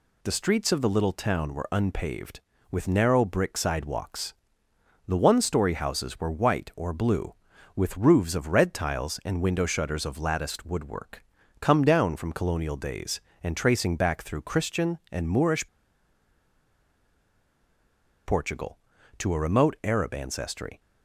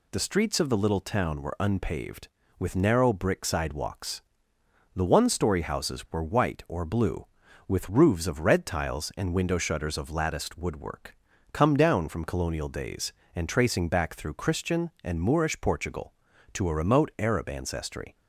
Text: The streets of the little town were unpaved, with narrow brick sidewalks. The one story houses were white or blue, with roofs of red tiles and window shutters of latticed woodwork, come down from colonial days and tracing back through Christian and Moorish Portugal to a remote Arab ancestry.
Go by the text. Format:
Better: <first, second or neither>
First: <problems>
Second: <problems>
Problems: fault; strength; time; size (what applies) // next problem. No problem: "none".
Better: second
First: pauses between "Moorish" and "Portugal"; strong; at 15.6 s; 2.5 s long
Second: none